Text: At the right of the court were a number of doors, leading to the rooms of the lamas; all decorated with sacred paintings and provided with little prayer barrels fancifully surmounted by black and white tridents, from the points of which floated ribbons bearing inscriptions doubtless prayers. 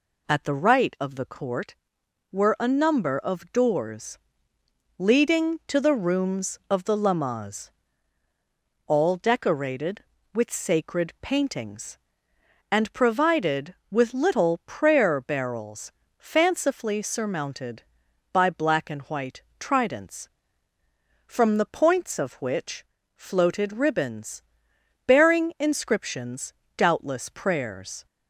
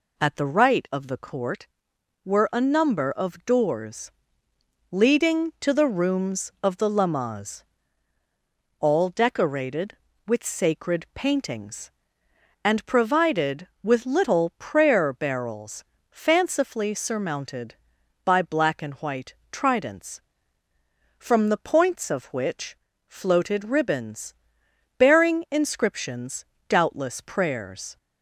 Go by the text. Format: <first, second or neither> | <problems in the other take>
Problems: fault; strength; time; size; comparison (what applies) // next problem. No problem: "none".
neither | pauses between "barrels" and "fancifully"; slight; the same in both // pauses between "white" and "tridents"; slight; the same in both // pauses between "which" and "floated"; slight; the same in both // pauses between "ribbons" and "bearing"; noticeable; the same in both // pauses between "inscriptions" and "doubtless"; slight; the same in both